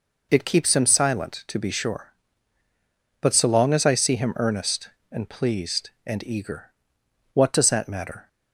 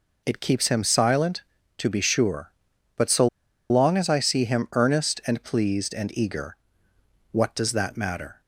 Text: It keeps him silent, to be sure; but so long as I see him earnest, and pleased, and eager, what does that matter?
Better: first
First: none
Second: pauses between "so" and "long"; at 3.2 s; 0.42 s long

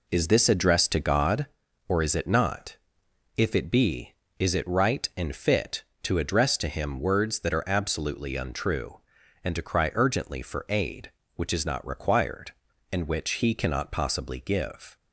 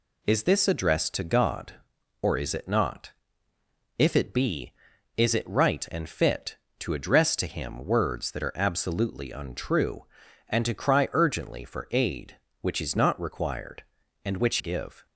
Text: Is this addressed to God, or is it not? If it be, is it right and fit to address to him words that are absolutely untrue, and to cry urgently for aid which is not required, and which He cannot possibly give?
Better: first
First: none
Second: skips "He cannot possibly"; at 14.5 s

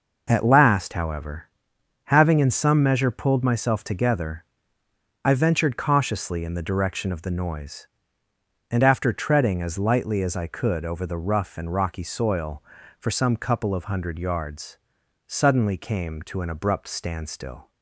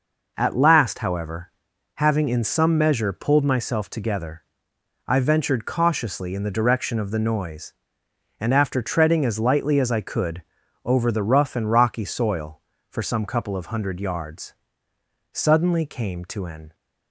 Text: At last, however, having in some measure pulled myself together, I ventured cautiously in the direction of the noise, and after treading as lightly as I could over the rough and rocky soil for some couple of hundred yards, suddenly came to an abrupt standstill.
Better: first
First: none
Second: pauses between "could" and "over"; at 10.4 s; 0.42 s long // stops before "abrupt standstill"; at 16.7 s

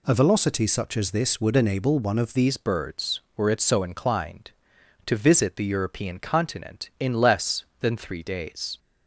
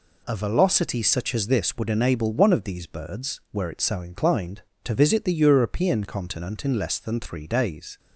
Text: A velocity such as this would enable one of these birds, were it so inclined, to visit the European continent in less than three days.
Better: second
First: changes voice at "these"; from 2.3 s on; 6.4 s long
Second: none

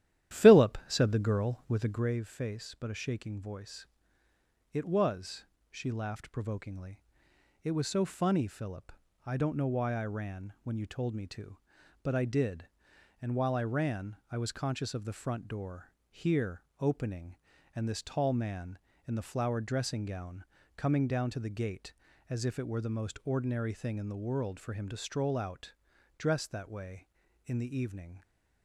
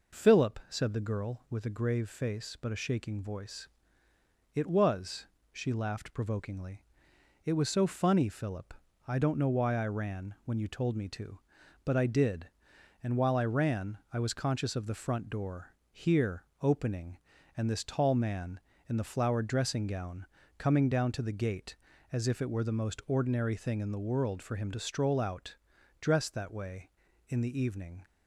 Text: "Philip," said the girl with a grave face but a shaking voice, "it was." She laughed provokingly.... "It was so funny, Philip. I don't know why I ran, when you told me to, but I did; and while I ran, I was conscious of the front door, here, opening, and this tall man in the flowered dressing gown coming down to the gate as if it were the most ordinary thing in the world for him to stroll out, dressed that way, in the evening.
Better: second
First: starts louder than the rest; strong; until 2.2 s; 12 dB // pauses between "gown" and "coming"; slight; at 20.4 s; 0.32 s long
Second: pauses between "gown" and "coming"; slight; at 20.2 s; 0.32 s long

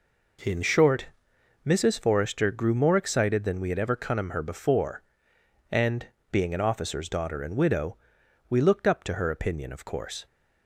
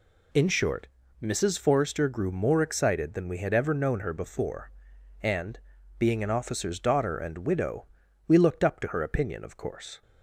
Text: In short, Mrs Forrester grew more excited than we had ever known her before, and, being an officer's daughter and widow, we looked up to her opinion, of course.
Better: second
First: says "cunnum" for "known"; at 3.9 s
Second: none

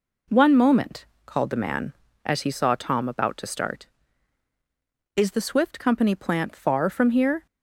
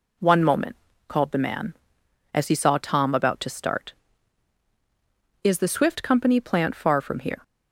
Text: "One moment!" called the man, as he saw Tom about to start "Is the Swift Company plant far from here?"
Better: neither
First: none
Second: none

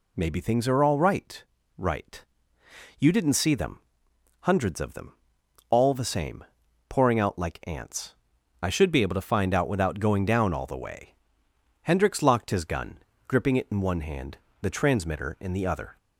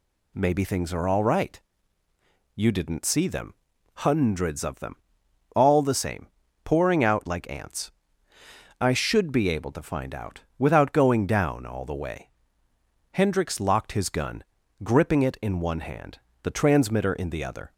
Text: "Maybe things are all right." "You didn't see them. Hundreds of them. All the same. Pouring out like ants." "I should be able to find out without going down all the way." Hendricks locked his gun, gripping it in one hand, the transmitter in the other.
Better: second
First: says "right" twice; at 1.7 s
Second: none

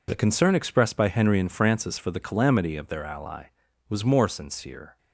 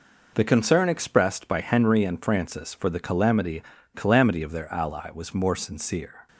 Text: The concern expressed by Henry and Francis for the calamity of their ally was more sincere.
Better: first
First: none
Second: says "calamity" twice; at 3.9 s

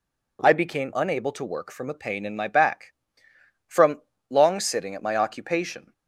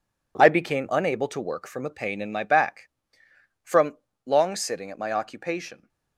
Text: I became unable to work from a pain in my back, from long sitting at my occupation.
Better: first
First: pauses between "from" and "long"; slight; at 4.0 s; 0.30 s long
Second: gets quieter; strong; throughout; 9.5 dB // pauses between "from" and "long"; slight; at 3.9 s; 0.30 s long

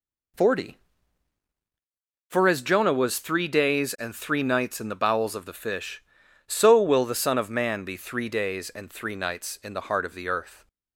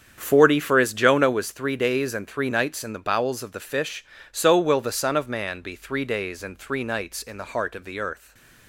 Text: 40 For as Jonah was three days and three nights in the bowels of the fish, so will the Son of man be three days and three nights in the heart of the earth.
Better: first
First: none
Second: starts louder than the rest; strong; until 1.5 s; 8 dB // stays silent after the last word; slight; from 8.1 s on; 0.5 s long

